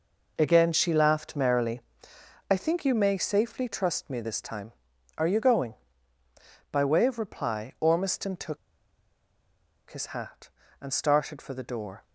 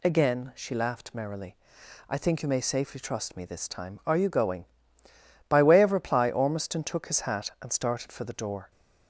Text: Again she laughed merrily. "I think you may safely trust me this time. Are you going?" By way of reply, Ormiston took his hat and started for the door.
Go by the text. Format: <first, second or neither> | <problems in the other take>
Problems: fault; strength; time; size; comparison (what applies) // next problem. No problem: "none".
second | pauses between "took" and "his"; strong; at 8.5 s; 1.3 s long